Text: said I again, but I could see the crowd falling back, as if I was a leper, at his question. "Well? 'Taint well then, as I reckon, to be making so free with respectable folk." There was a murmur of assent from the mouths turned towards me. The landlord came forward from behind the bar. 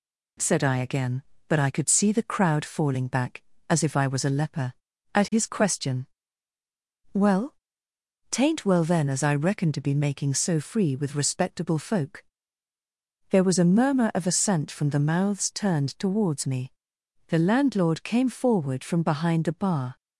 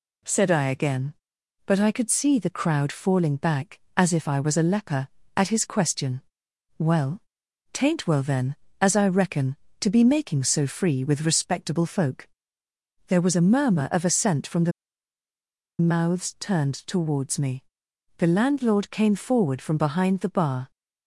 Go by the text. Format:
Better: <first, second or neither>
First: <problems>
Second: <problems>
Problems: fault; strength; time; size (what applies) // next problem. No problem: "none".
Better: first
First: none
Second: pauses between "the" and "mouths"; at 14.7 s; 1.0 s long